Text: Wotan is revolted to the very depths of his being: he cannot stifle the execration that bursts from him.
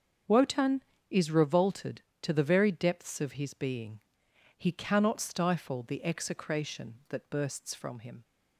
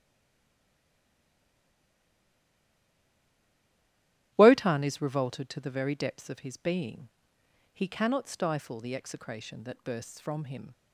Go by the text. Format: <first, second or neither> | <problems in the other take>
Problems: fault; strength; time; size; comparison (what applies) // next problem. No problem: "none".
first | stays silent before the first word; strong; until 4.3 s; 4.3 s long // starts louder than the rest; strong; until 5.3 s; 12.5 dB; also in the first